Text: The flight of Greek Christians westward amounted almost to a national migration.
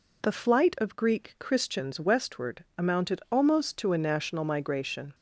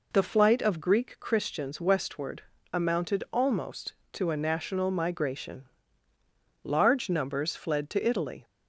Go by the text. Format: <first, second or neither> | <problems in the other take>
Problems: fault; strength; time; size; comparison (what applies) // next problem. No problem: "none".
first | pauses between "westward" and "amounted"; slight; at 2.4 s; 0.28 s long // goes on to say "Large numbers fled to Italy"; strong; from 6.6 s on; 1.8 s long